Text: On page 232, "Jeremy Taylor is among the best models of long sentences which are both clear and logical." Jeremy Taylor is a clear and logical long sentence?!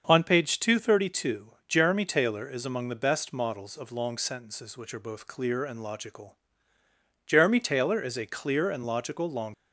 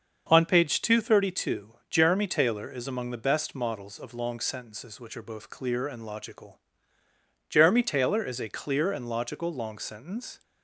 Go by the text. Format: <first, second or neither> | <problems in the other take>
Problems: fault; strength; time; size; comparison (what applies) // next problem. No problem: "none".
second | starts louder than the rest; until 1.0 s; 6.5 dB; also in the second // stops before "sentence"; at 9.5 s